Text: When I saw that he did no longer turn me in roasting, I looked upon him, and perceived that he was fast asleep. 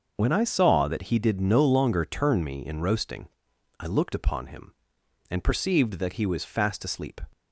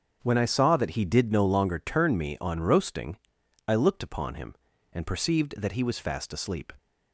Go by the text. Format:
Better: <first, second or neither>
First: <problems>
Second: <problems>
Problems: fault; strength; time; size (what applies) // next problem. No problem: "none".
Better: first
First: starts louder than the rest; until 1.1 s; 6.5 dB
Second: starts louder than the rest; strong; until 1.2 s; 7.5 dB // says "on" for "in"; at 2.4 s